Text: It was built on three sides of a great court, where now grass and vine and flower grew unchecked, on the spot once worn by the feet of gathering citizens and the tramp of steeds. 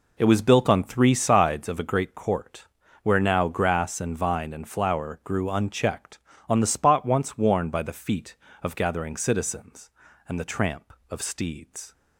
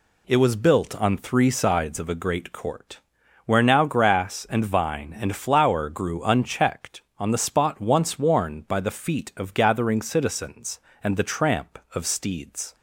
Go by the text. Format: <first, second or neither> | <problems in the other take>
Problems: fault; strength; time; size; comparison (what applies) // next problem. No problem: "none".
second | starts louder than the rest; until 1.6 s; 4 dB